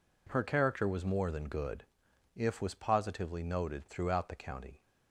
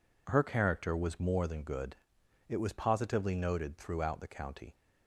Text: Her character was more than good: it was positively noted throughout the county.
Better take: second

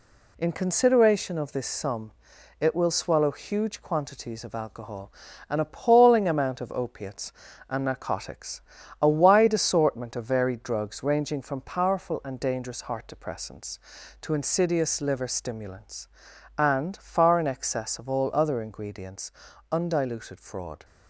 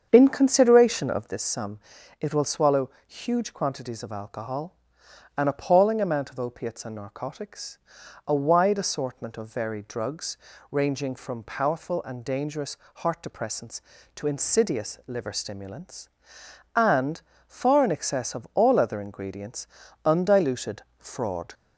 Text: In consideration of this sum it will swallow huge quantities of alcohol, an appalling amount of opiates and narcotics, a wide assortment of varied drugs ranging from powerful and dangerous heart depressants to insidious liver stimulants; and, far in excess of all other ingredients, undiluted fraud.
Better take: first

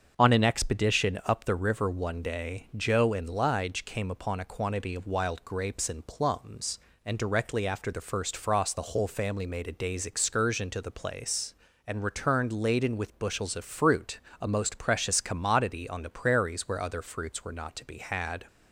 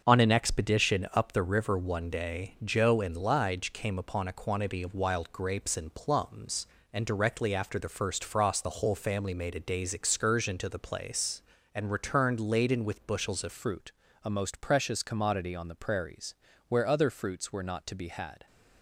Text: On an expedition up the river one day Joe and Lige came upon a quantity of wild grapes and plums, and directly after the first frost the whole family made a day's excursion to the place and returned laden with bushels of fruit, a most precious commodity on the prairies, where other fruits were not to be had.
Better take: first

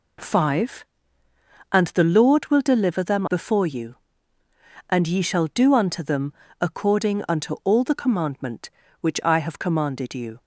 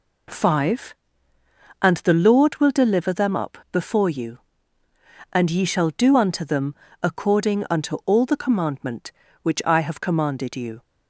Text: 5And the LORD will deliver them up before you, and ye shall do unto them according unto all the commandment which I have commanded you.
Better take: second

